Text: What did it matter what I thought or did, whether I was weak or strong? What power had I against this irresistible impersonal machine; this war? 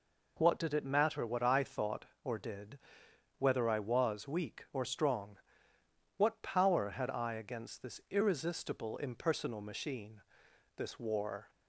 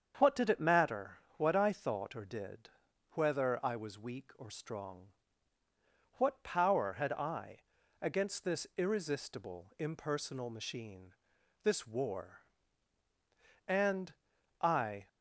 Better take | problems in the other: first | starts louder than the rest; strong; until 1.1 s; 7.5 dB // pauses between "matter" and "what"; slight; at 1.1 s; 0.18 s long // pauses between "I" and "against"; at 7.5 s; 0.42 s long // goes on to say "And I"; from 13.6 s on; 1.4 s long

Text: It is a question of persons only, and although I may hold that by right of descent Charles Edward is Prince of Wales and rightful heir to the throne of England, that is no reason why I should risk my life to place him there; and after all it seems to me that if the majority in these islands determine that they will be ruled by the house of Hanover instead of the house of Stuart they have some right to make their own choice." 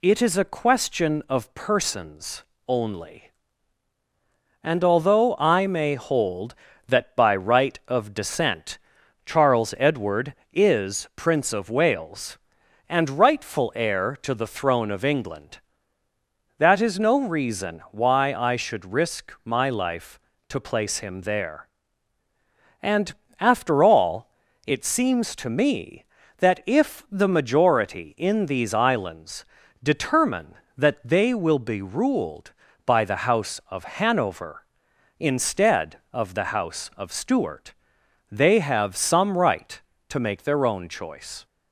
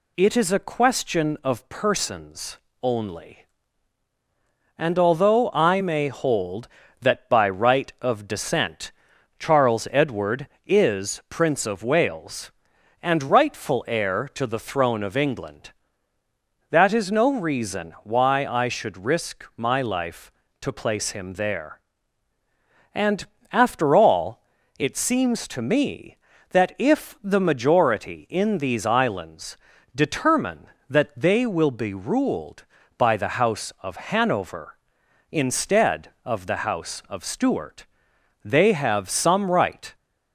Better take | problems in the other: first | pauses between "persons" and "only"; slight; at 2.5 s; 0.24 s long; slight in the first // pauses between "descent" and "Charles"; noticeable; at 8.9 s; 0.48 s long; noticeable in the first // pauses between "and" and "after"; slight; at 23.2 s; 0.26 s long; slight in the first // pauses between "all" and "it"; slight; at 24.4 s; 0.36 s long; slight in the first // pauses between "islands" and "determine"; at 29.5 s; 0.38 s long; also in the first // pauses between "Stuart" and "they"; noticeable; at 37.8 s; 0.58 s long; noticeable in the first // stops before "to make their own choice"; at 39.9 s

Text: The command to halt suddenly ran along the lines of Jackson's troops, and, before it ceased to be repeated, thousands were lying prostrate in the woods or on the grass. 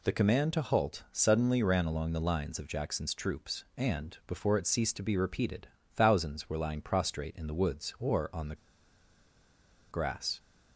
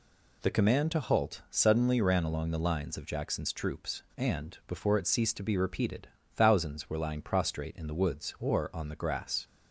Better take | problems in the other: second | pauses between "the" and "grass"; strong; at 8.5 s; 1.3 s long

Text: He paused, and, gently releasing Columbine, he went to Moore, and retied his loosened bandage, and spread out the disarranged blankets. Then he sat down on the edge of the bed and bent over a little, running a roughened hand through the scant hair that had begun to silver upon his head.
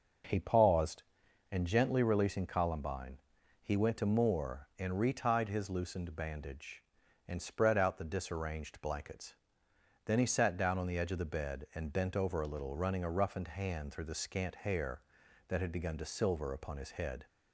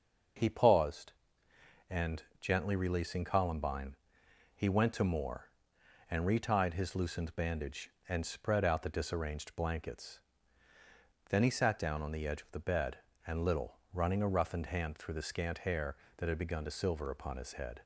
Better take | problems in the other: first | starts louder than the rest; until 2.1 s; 6 dB // skips "bent over a"; at 13.4 s

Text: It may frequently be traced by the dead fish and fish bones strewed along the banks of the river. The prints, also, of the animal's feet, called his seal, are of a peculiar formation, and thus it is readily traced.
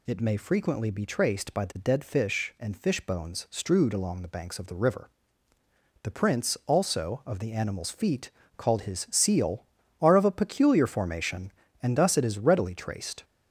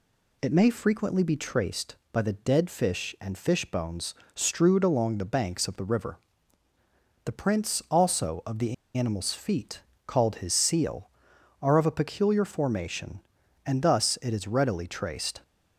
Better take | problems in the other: first | pauses between "bones" and "strewed"; slight; at 4.1 s; 0.22 s long // pauses between "the" and "animal's"; slight; at 8.7 s; 0.22 s long

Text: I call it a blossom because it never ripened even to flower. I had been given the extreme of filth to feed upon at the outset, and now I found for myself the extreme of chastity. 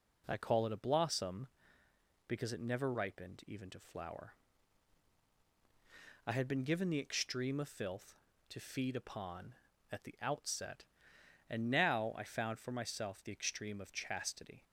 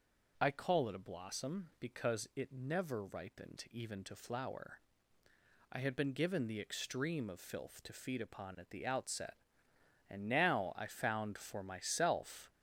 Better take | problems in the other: first | stops before "the extreme of chastity"; at 12.5 s

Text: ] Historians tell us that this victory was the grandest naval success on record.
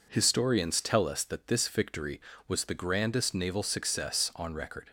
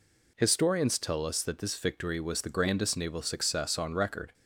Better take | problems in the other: neither | none

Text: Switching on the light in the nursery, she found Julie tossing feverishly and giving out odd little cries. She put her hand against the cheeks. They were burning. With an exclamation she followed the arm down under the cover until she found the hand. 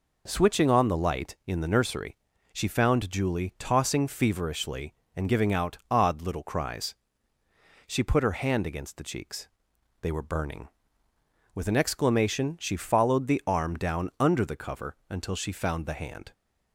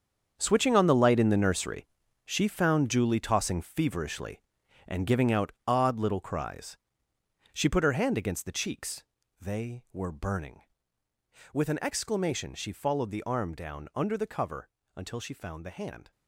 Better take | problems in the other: first | gets quieter; strong; throughout; 12 dB // pauses between "cover" and "until"; slight; at 14.6 s; 0.28 s long

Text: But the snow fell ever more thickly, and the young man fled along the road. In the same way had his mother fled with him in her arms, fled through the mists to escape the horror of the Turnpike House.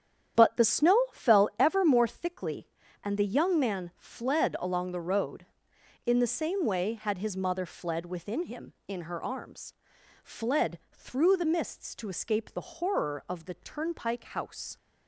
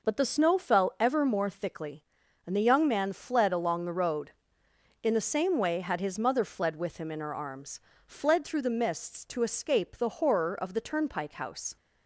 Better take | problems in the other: second | starts louder than the rest; strong; until 1.6 s; 9.5 dB // says "within" for "with"; at 8.0 s

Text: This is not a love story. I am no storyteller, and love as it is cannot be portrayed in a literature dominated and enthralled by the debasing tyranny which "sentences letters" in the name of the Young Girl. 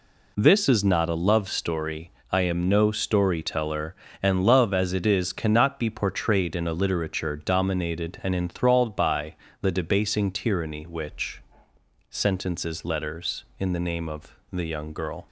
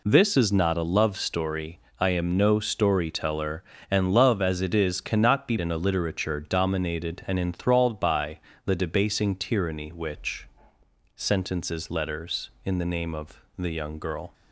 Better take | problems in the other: first | skips "portrayed"; at 5.5 s // pauses between "by" and "the"; slight; at 8.3 s; 0.26 s long; slight in the first // pauses between "which" and "sentences"; noticeable; at 10.4 s; 0.68 s long; noticeable in the first // pauses between "of" and "the"; slight; at 13.4 s; 0.16 s long; slight in the first

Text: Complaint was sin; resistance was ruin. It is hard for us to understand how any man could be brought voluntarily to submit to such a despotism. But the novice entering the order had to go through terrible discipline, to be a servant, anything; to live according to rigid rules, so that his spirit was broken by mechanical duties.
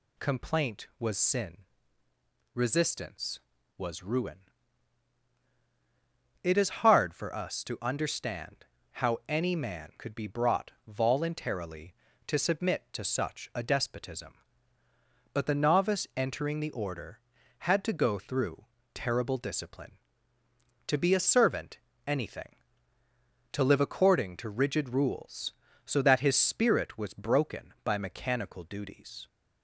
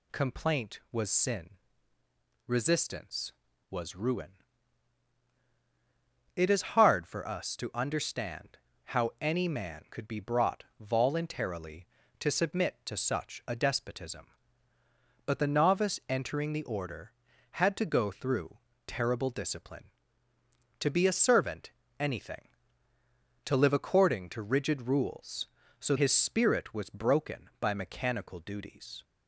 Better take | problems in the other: first | pauses between "understand" and "how"; slight; at 8.5 s; 0.28 s long; slight in the first // pauses between "brought" and "voluntarily"; slight; at 10.6 s; 0.16 s long; slight in the first // pauses between "through" and "terrible"; slight; at 18.5 s; 0.30 s long; slight in the first // skips "that"; at 25.9 s

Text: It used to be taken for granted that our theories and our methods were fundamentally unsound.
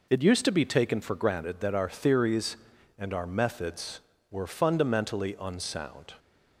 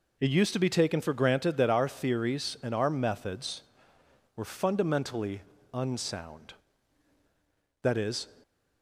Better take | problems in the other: first | pauses between "fundamentally" and "unsound"; slight; at 5.4 s; 0.30 s long // goes on to say "That is"; slight; from 7.8 s on; 0.46 s long

